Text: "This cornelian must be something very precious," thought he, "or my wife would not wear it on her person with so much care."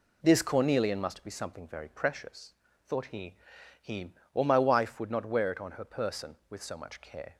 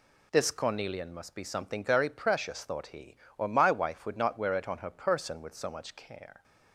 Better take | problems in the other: second | says "he" twice; at 3.8 s

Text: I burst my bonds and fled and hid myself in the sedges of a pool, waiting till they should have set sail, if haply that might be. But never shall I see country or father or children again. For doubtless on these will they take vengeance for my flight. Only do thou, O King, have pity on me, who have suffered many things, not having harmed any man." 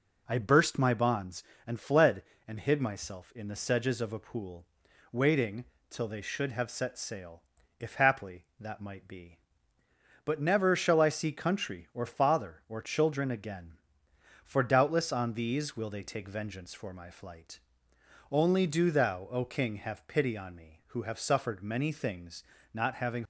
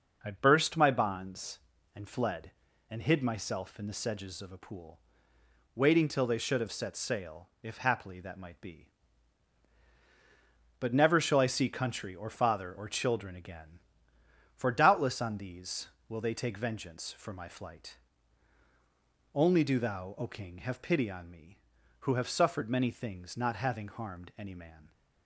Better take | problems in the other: second | pauses between "waiting" and "till"; slight; at 5.6 s; 0.24 s long // stops before "harmed any man"; at 23.2 s

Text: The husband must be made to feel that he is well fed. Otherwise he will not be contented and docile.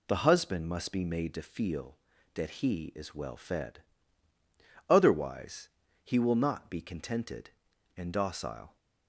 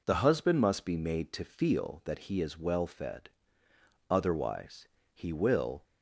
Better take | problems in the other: first | pauses between "Otherwise" and "he"; slight; at 4.8 s; 0.26 s long; slight in the first // stops before "not be contented and docile"; at 5.8 s

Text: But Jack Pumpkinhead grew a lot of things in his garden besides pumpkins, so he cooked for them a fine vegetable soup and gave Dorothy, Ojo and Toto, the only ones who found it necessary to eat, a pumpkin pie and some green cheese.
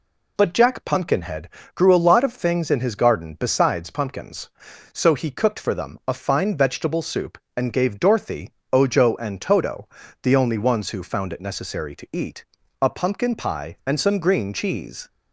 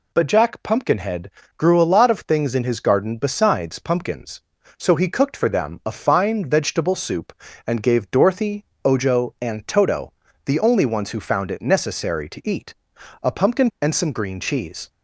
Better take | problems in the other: first | pauses between "Pumpkinhead" and "grew"; slight; at 1.3 s; 0.28 s long; slight in the first // skips "pie"; at 13.7 s

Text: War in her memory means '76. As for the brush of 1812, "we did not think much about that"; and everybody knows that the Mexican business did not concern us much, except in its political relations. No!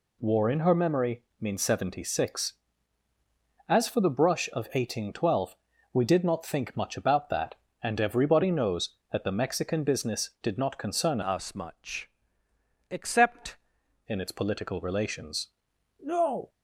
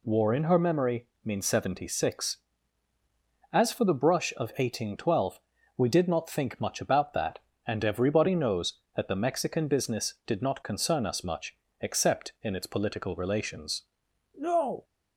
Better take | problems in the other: second | pauses between "memory" and "means"; slight; at 1.2 s; 0.16 s long; slight in the second // changes voice from "us" to "except"; from 11.2 to 13.5 s; 2.3 s long

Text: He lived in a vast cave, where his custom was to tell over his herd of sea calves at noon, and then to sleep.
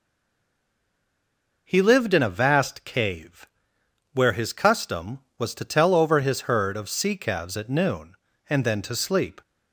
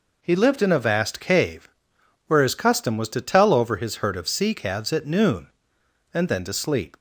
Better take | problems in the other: second | stays silent before the first word; noticeable; until 1.6 s; 1.6 s long

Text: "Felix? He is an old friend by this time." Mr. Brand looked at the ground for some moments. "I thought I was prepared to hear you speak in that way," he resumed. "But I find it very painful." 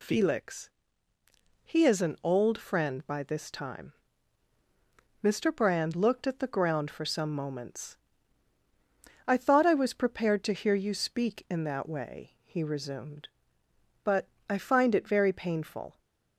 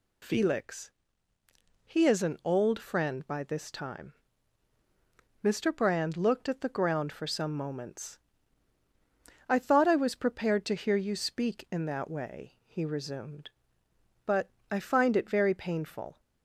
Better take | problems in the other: neither | pauses between "But" and "I"; slight; the same in both

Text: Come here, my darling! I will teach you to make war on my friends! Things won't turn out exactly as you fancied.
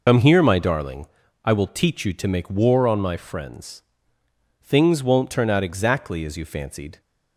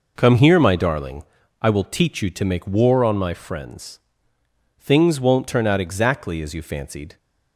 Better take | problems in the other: second | loses the start of "Come"; at 0.0 s; 70 ms

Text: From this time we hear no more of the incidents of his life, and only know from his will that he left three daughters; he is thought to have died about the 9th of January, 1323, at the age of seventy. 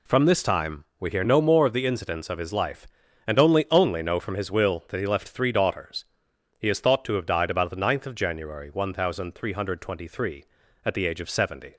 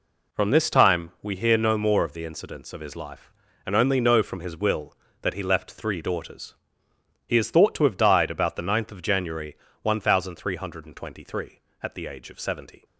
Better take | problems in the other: second | pauses between "time" and "we"; slight; at 0.8 s; 0.16 s long // says "only" twice; at 3.7 s

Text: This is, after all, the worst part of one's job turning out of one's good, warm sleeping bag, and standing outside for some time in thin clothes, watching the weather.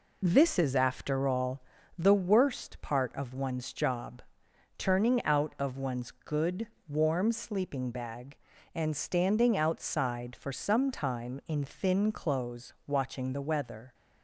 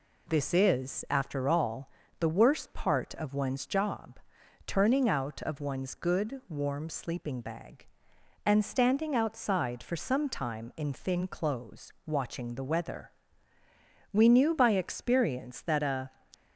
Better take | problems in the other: first | pauses between "job" and "turning"; noticeable; at 4.1 s; 0.48 s long; noticeable in the first // goes on to say "We knew by experience that a"; strong; from 14.1 s on; 1.9 s long

